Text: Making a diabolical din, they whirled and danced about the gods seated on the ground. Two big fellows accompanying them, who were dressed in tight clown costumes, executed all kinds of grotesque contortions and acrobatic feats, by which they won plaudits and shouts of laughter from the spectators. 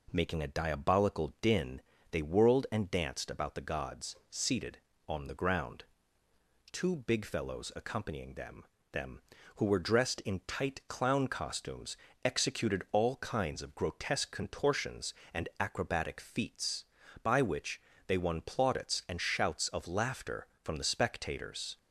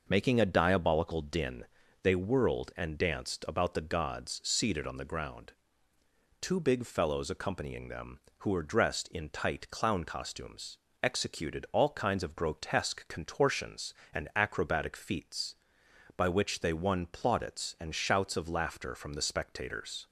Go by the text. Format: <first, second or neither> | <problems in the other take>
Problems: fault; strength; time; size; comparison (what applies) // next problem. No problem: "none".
second | says "them" twice; at 8.9 s // pauses between "which" and "they"; slight; at 17.7 s; 0.28 s long